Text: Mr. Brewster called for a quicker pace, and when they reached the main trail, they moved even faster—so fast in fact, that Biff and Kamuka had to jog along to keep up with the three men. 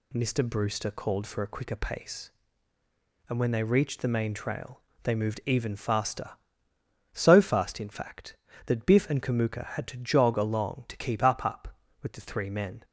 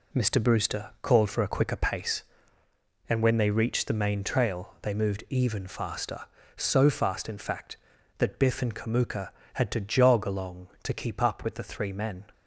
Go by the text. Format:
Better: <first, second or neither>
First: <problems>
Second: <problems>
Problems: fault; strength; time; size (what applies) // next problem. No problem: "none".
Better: second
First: says "up" twice; at 11.4 s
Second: none